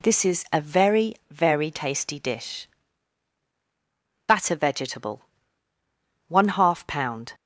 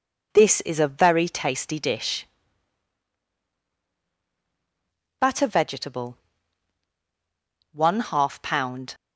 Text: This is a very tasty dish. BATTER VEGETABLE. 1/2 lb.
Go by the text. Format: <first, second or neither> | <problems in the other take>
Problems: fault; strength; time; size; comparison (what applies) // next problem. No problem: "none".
second | says "very" twice; at 1.2 s